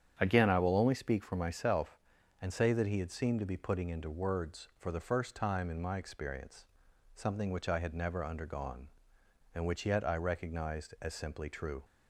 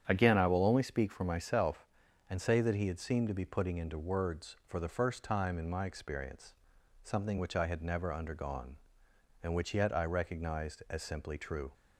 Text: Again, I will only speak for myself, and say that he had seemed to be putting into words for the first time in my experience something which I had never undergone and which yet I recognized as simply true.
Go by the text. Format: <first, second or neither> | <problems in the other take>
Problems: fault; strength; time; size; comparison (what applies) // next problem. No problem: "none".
neither | starts louder than the rest; strong; the same in both // pauses between "experience" and "something"; noticeable; the same in both